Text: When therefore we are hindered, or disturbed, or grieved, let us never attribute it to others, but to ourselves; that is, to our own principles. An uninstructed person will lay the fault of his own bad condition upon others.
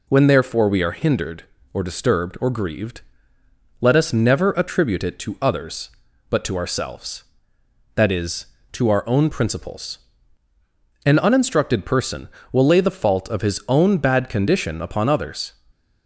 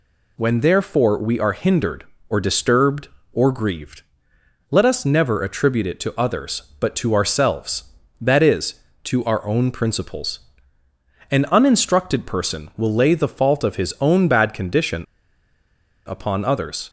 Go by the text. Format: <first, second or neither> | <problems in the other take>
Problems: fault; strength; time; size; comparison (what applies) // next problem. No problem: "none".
first | pauses between "condition" and "upon"; at 15.0 s; 1.0 s long